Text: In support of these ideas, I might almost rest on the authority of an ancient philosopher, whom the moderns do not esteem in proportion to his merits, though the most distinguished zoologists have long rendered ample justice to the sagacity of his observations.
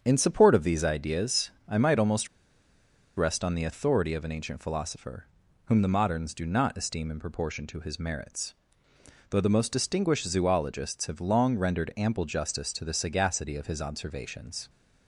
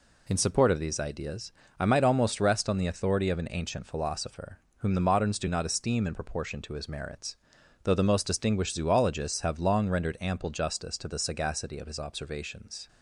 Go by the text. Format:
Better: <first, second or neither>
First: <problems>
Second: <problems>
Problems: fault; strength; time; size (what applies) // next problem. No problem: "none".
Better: second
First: starts louder than the rest; strong; until 1.0 s; 7.5 dB // pauses between "almost" and "rest"; noticeable; at 2.2 s; 0.90 s long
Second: none